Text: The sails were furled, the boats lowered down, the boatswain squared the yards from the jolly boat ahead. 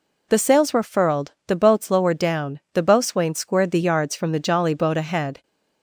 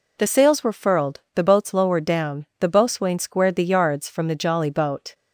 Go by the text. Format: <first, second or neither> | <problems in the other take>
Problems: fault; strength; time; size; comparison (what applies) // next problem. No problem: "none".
first | stops before "ahead"; at 5.1 s